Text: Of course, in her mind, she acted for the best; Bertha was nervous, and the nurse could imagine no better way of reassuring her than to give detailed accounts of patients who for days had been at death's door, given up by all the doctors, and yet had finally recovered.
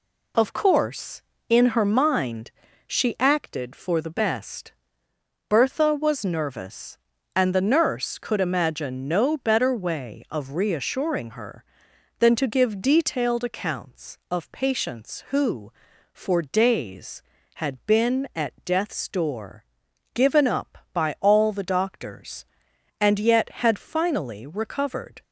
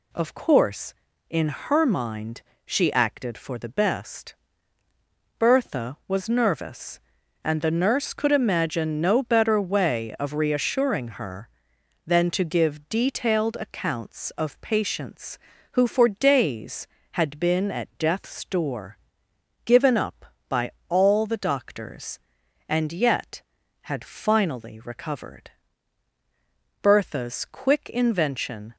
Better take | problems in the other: first | pauses between "by" and "all"; slight; at 20.6 s; 0.20 s long // goes on to say "Bertha's quick invention"; strong; from 26.8 s on; 1.9 s long

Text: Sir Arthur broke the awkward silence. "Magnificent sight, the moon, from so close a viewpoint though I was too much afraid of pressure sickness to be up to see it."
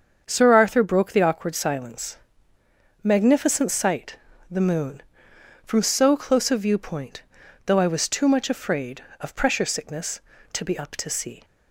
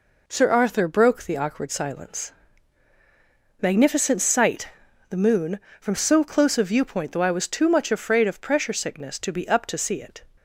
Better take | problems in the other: second | starts louder than the rest; until 1.2 s; 7 dB // pauses between "viewpoint" and "though"; noticeable; at 7.2 s; 0.46 s long // stops before "it"; at 11.4 s

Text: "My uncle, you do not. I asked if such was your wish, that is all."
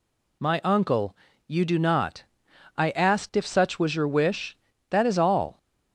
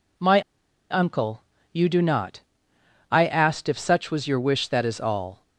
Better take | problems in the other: first | pauses between "My" and "uncle"; noticeable; at 0.4 s; 0.49 s long

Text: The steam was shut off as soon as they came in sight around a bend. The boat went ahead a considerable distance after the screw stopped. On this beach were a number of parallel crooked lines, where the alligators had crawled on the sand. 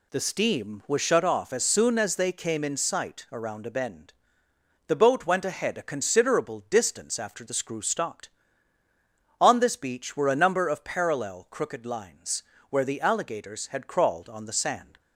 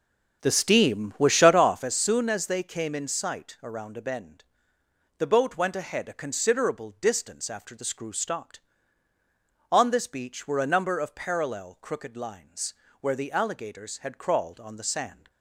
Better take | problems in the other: first | starts louder than the rest; strong; until 2.0 s; 7.5 dB

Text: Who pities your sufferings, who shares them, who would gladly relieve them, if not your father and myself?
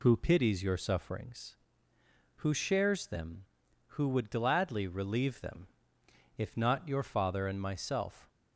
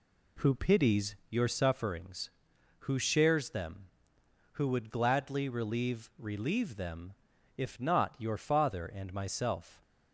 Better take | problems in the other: first | pauses between "pities" and "your"; slight; at 1.1 s; 0.16 s long // says "relieve" twice; at 6.1 s

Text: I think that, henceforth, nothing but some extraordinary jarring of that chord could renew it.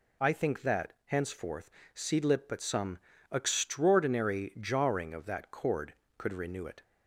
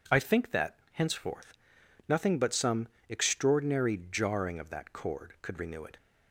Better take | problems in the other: second | says "seedlip" for "nothing"; at 1.9 s // pauses between "some" and "extraordinary"; slight; at 2.9 s; 0.34 s long; slight in the second

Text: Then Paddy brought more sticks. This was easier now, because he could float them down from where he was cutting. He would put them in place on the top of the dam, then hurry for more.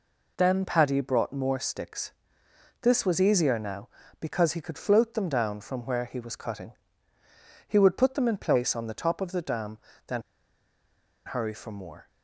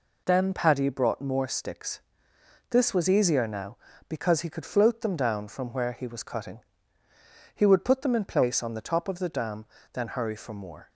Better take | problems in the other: second | pauses between "then" and "hurry"; at 10.2 s; 1.0 s long

